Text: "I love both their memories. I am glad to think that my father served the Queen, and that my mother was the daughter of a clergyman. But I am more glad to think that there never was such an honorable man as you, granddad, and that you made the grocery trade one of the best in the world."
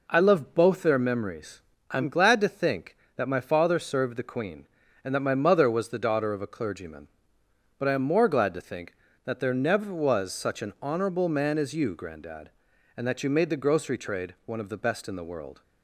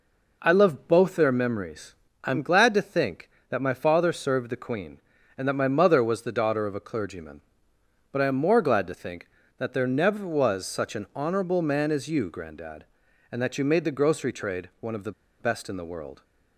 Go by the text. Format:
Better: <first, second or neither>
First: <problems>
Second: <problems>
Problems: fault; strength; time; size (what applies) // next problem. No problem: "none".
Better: first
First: none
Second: pauses between "the" and "best"; slight; at 15.1 s; 0.28 s long